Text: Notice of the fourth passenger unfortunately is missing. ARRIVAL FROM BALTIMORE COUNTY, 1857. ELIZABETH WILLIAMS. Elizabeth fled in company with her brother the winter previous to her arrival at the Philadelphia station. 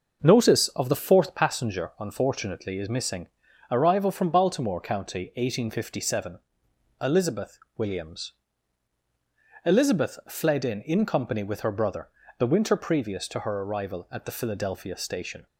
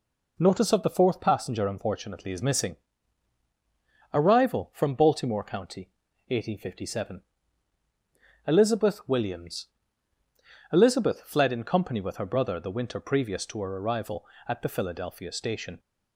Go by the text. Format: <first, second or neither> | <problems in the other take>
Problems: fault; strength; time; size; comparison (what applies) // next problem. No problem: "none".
second | starts louder than the rest; noticeable; until 1.3 s; 6 dB // pauses between "ELIZABETH" and "WILLIAMS"; slight; at 7.5 s; 0.20 s long // says "in" twice; at 10.8 s // pauses between "brother" and "the"; slight; at 12.0 s; 0.28 s long